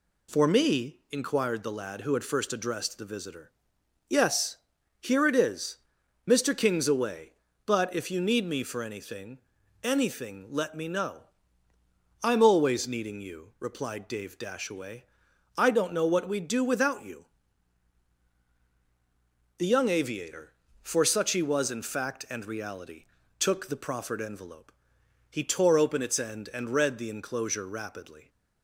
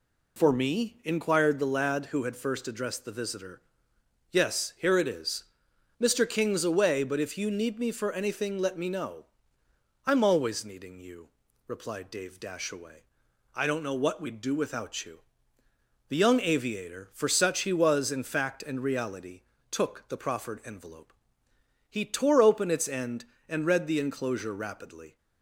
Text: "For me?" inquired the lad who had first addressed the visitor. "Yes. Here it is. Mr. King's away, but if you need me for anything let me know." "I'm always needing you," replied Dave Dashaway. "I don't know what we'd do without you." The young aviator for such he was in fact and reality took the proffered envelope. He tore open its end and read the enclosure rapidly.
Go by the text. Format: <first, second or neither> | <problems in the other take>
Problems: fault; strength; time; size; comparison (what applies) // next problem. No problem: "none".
second | says "anything" twice; at 9.8 s // pauses between "reality" and "took"; slight; at 23.0 s; 0.34 s long; slight in the second